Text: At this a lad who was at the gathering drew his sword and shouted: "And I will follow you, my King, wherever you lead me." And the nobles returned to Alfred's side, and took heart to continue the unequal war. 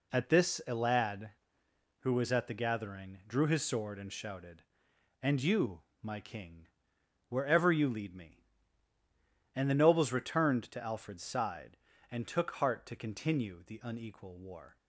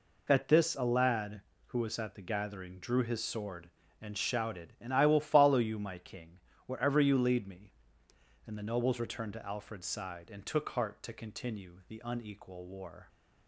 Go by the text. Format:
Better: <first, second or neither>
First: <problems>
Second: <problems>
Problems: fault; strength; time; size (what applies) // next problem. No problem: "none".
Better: second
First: skips "I will follow"; at 5.4 s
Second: none